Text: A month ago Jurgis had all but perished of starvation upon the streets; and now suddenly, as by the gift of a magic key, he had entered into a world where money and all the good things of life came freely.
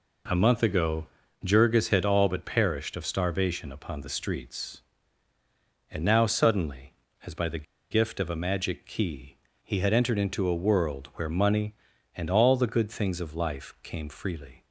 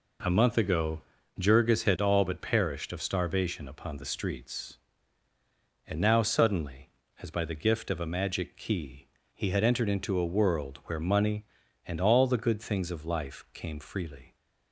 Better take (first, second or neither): second